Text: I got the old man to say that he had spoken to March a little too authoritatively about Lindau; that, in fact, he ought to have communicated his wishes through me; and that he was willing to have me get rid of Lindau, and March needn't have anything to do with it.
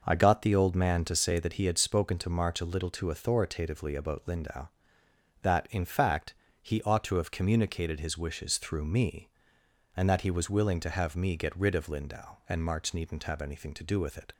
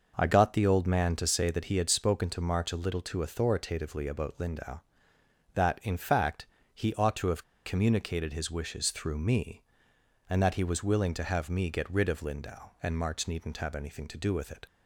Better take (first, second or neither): first